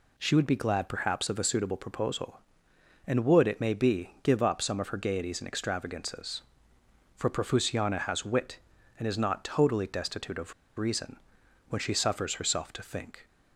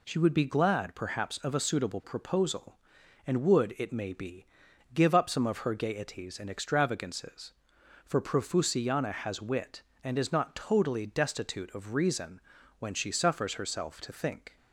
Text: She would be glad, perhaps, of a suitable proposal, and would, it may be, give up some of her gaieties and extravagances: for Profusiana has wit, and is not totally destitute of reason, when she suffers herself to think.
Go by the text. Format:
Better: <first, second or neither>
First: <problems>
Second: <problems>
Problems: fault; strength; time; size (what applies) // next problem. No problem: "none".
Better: second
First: pauses between "of" and "reason"; slight; at 10.5 s; 0.25 s long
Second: none